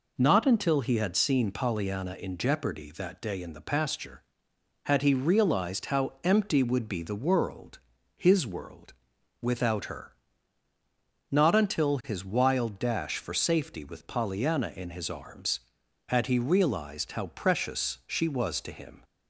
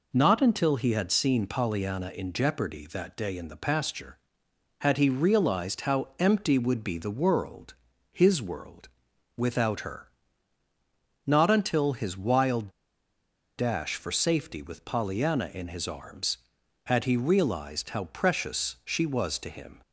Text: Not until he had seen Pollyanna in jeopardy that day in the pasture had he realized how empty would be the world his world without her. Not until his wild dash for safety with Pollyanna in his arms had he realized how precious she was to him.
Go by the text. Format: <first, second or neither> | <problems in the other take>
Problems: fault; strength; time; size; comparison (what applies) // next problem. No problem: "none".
first | pauses between "world" and "his"; slight; at 7.7 s; 0.36 s long; slight in the first // pauses between "world" and "without"; noticeable; at 8.8 s; 0.48 s long; noticeable in the first // pauses between "wild" and "dash"; noticeable; at 12.7 s; 0.86 s long